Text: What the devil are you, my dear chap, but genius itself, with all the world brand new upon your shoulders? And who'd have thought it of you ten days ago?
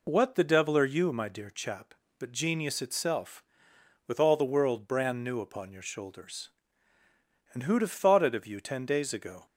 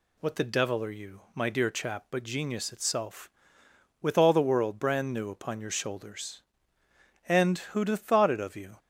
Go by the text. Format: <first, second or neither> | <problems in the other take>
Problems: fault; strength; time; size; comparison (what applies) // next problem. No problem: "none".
first | stops before "ten days ago"; at 8.7 s